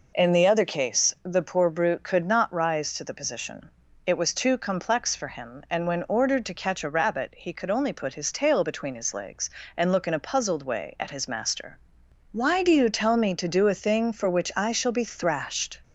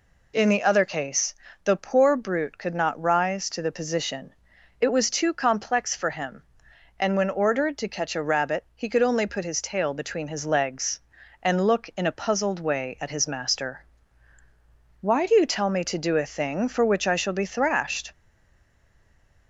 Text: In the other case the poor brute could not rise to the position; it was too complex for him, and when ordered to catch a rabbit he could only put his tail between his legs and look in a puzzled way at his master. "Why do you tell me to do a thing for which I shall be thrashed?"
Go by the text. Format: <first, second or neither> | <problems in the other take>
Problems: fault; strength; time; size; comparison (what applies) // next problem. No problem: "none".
first | pauses between "case" and "the"; slight; at 1.3 s; 0.30 s long // stays silent after the last word; noticeable; from 18.1 s on; 1.3 s long